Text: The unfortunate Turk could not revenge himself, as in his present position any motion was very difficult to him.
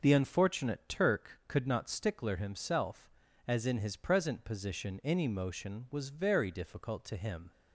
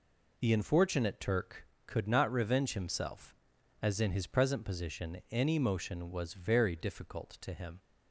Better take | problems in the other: second | says "stickler" for "revenge"; at 1.8 s

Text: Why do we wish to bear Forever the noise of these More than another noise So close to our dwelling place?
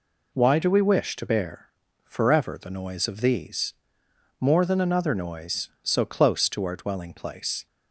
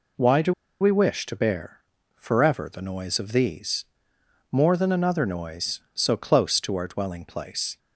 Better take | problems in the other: first | pauses between "do" and "we"; slight; at 0.5 s; 0.27 s long // pauses between "bear" and "Forever"; slight; at 1.8 s; 0.34 s long; slight in the first // pauses between "these" and "More"; noticeable; at 3.8 s; 0.66 s long; noticeable in the first

